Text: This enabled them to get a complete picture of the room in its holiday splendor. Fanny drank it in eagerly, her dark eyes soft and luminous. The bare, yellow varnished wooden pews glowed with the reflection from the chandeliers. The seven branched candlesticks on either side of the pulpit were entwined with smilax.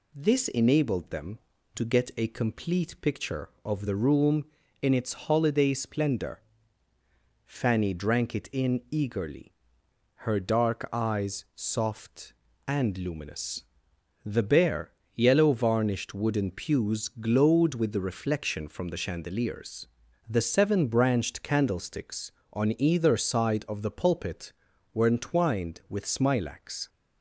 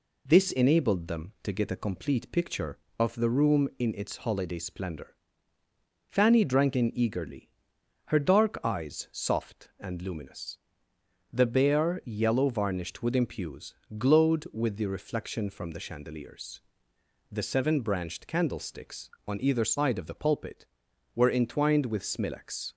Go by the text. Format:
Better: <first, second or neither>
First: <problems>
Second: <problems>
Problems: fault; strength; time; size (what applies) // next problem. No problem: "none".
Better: first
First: none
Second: skips "it"; at 6.7 s // pauses between "pews" and "glowed"; slight; at 13.7 s; 0.22 s long